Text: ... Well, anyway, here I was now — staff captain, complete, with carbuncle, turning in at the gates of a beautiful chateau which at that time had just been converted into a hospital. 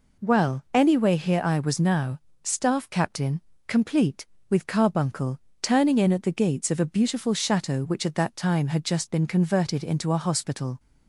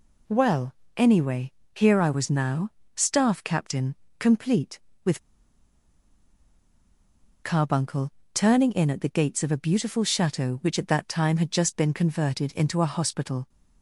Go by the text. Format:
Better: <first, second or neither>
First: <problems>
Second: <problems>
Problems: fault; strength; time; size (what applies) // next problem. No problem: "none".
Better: first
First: none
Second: pauses between "with" and "carbuncle"; strong; at 5.2 s; 2.2 s long